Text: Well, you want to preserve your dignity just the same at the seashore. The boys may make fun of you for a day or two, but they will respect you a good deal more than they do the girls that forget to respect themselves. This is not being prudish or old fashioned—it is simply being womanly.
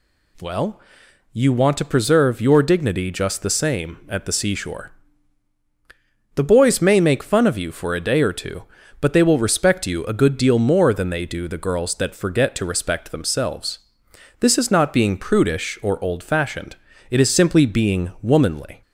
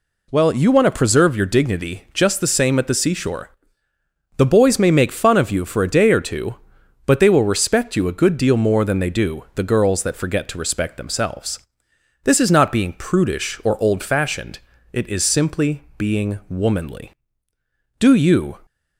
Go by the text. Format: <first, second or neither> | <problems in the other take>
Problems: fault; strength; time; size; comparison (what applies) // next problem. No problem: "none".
first | goes on to say "Do you"; from 17.9 s on; 0.60 s long